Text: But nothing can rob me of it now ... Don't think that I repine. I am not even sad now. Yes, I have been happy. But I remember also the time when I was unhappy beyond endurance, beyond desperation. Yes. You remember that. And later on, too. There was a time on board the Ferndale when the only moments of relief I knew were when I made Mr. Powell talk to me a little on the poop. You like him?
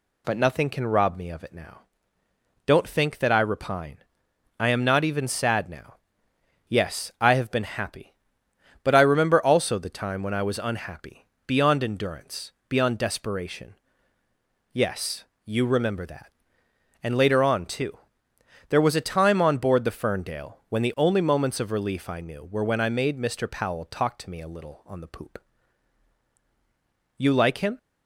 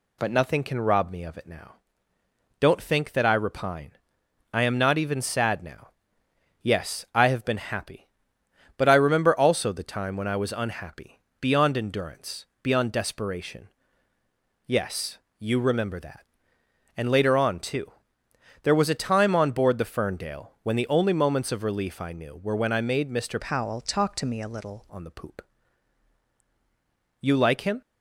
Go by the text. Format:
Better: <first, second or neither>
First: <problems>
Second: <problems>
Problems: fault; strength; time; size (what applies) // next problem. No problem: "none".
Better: first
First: pauses between "unhappy" and "beyond"; slight; at 11.2 s; 0.18 s long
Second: pauses between "unhappy" and "beyond"; slight; at 11.2 s; 0.18 s long // changes voice from "Powell" to "little"; from 23.4 to 24.8 s; 1.4 s long